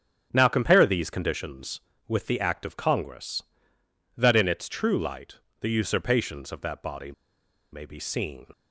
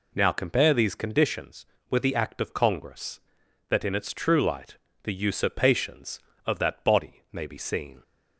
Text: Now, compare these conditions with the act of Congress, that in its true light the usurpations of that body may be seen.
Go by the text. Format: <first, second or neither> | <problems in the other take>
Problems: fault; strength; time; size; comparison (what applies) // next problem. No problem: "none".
second | starts louder than the rest; strong; until 1.3 s; 8 dB // pauses between "light" and "the"; slight; at 5.3 s; 0.20 s long; slight in the second // pauses between "body" and "may"; noticeable; at 7.1 s; 0.60 s long